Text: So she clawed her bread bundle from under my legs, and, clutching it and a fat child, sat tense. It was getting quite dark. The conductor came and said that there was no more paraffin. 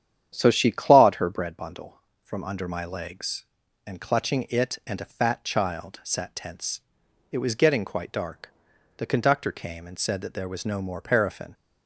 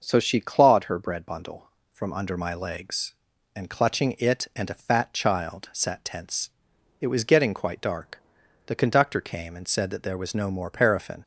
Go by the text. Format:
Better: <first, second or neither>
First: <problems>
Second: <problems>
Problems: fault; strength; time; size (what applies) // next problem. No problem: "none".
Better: second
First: starts louder than the rest; strong; until 1.6 s; 9.5 dB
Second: none